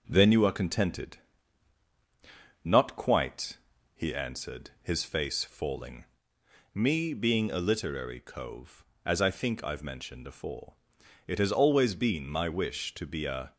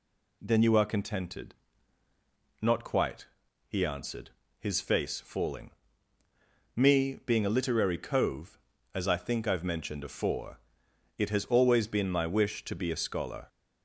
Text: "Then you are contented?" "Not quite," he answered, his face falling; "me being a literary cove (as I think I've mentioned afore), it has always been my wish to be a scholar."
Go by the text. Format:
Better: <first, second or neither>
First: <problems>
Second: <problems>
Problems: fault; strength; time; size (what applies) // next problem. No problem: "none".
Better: second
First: stops before "scholar"; at 13.5 s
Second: none